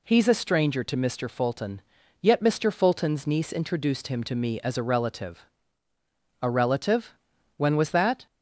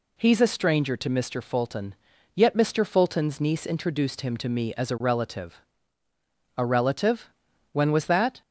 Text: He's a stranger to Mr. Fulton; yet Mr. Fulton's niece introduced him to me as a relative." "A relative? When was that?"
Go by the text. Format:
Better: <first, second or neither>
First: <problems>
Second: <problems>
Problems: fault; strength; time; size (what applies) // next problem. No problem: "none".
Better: neither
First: none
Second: none